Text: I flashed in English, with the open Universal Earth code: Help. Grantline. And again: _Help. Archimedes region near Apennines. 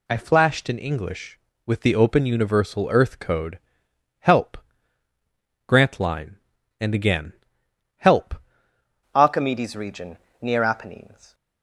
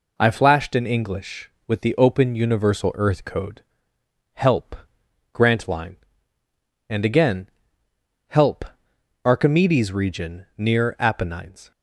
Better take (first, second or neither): second